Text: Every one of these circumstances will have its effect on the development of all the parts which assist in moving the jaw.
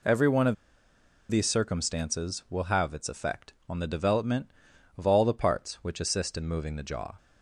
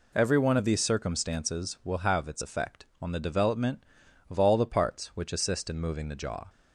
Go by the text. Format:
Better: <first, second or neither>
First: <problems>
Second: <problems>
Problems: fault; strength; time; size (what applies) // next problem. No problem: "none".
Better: second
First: pauses between "of" and "these"; noticeable; at 0.5 s; 0.76 s long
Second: none